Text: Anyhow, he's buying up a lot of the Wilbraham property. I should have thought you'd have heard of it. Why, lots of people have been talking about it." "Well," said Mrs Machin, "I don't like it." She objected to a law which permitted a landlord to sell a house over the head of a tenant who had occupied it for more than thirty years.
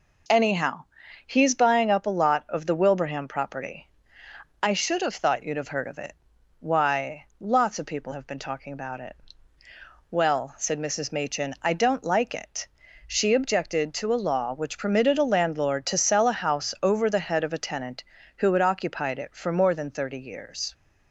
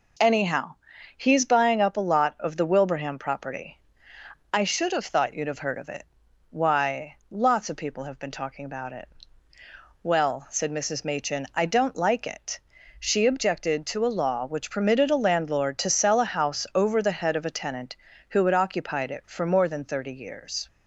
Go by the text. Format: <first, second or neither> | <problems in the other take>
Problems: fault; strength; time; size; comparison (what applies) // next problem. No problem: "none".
neither | none